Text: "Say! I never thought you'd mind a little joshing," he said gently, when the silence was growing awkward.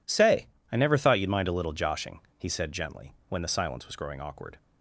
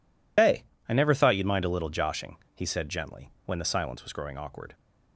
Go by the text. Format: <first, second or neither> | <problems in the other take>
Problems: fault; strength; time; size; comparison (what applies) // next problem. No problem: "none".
first | loses the start of "Say"; at 0.3 s; 160 ms